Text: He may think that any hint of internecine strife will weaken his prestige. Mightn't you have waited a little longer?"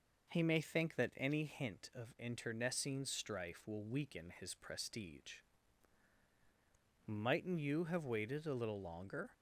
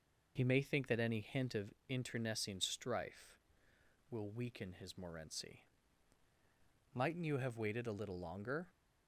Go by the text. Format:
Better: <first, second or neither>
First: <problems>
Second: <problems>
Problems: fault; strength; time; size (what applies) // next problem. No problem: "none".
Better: first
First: none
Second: pauses between "of" and "internecine"; slight; at 1.7 s; 0.16 s long // says "morency" for "prestige"; at 4.9 s